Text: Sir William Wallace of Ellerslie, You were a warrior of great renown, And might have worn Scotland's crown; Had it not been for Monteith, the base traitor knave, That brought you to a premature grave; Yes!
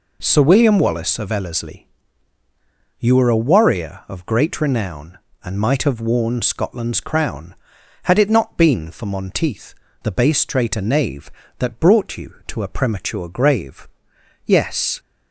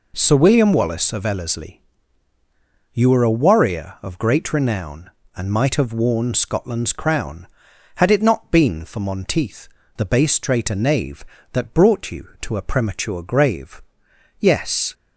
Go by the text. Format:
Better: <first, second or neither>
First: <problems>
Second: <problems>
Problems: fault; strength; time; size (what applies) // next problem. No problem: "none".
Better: neither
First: none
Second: none